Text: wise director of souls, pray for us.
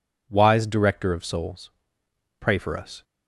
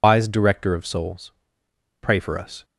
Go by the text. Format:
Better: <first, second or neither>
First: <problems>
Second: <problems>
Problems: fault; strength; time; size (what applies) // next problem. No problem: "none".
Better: first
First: none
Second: loses the start of "wise"; at 0.0 s; 130 ms